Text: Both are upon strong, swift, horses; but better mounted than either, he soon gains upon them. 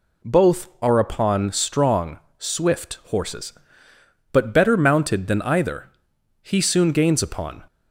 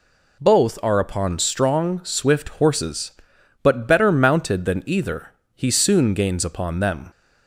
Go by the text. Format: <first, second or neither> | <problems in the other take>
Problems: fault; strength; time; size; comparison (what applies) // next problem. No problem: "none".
second | stops before "them"; at 7.6 s